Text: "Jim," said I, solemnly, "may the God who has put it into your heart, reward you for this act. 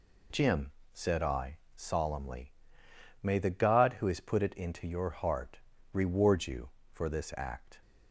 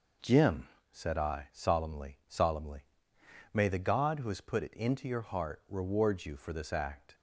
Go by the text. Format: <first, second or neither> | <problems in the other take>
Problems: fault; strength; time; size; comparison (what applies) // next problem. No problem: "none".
first | says "solemnly" twice; at 2.2 s